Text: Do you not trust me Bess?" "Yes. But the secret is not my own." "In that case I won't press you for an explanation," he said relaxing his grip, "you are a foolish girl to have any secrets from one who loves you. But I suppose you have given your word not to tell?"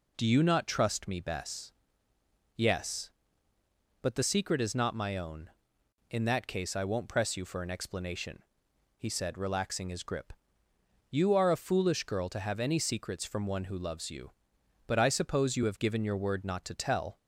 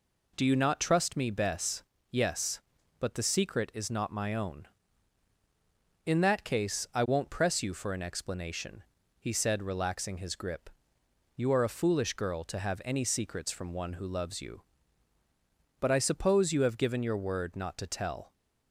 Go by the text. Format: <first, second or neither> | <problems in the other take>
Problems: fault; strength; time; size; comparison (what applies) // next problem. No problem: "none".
neither | none